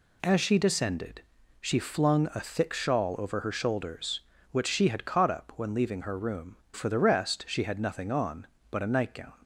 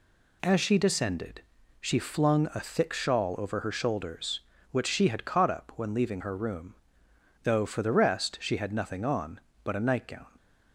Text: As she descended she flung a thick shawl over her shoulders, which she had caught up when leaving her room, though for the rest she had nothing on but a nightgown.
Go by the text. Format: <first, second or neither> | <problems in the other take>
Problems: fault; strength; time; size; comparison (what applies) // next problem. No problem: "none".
second | pauses between "descended" and "she"; at 1.2 s; 0.40 s long; also in the second // skips "though"; at 6.6 s